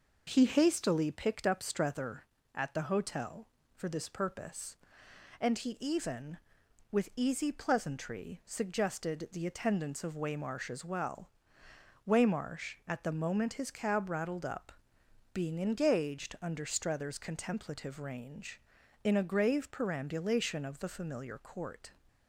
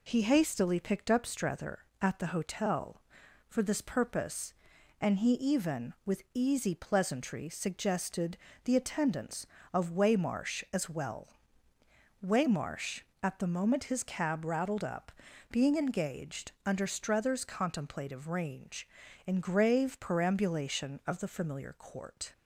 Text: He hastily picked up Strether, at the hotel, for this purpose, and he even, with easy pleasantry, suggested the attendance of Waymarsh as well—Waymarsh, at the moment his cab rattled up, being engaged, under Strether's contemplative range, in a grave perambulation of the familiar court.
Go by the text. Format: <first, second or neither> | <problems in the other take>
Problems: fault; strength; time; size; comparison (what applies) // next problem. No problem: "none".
first | pauses between "suggested" and "the"; slight; at 8.3 s; 0.26 s long // skips "a"; at 19.4 s